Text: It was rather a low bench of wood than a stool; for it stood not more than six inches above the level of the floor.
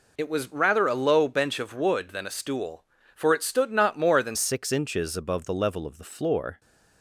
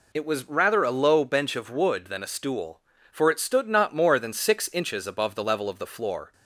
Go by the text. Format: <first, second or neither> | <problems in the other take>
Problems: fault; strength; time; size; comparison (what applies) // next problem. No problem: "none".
second | changes voice at "six"; from 4.3 s on; 2.2 s long